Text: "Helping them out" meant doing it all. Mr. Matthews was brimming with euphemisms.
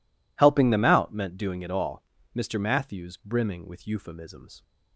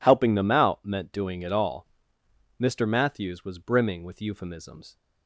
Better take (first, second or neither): second